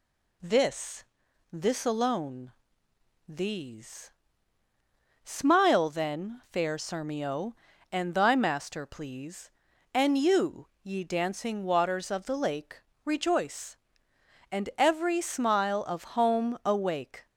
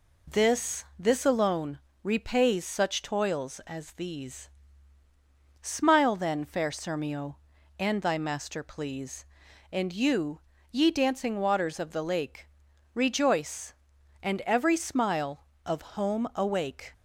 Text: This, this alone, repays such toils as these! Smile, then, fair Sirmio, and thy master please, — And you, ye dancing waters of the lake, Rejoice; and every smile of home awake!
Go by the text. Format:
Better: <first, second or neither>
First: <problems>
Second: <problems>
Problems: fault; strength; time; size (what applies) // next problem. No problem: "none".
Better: second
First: skips "repays such toils as"; at 2.8 s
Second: none